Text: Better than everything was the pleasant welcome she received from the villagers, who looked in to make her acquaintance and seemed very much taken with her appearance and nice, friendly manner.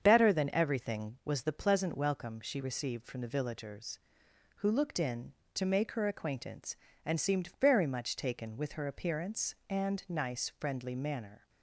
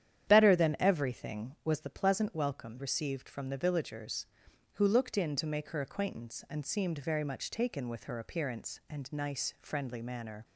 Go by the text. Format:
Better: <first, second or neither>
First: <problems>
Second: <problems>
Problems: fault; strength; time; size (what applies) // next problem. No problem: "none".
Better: first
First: starts louder than the rest; strong; until 1.0 s; 7.5 dB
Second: starts louder than the rest; strong; until 1.3 s; 10 dB // skips "she"; at 2.7 s